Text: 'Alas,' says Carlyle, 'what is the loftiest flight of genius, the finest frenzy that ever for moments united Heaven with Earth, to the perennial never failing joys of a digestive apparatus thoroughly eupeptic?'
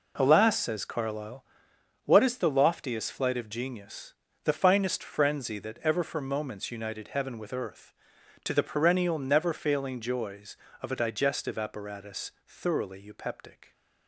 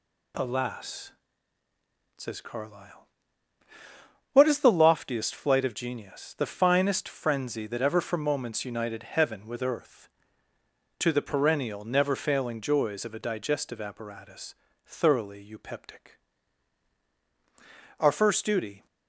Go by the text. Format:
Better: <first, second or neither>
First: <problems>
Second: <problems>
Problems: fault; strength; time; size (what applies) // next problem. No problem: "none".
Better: first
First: pauses between "apparatus" and "thoroughly"; slight; at 12.3 s; 0.16 s long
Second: pauses between "apparatus" and "thoroughly"; slight; at 14.5 s; 0.32 s long // goes on to say "Our first duty"; noticeable; from 17.9 s on; 0.88 s long